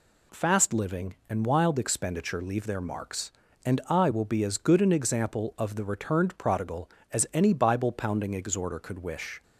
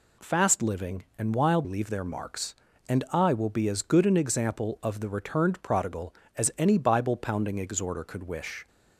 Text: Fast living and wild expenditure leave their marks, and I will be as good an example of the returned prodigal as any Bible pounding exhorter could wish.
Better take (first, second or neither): first